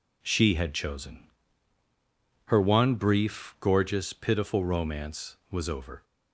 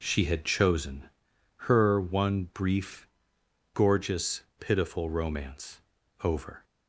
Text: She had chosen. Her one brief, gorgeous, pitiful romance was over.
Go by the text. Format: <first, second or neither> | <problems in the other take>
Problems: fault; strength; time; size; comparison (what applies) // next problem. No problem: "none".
first | skips "was"; at 6.0 s